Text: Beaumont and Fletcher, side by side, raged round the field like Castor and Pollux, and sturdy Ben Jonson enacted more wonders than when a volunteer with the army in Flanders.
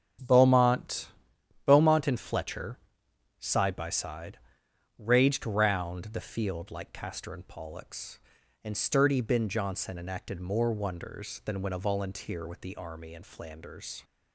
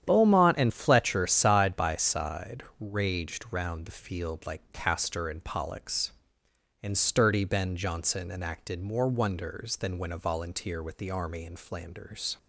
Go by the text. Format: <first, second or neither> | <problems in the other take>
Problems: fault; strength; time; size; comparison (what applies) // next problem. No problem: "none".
second | starts louder than the rest; strong; until 1.7 s; 8.5 dB; strong in the second // says "Beaumont" twice; at 1.6 s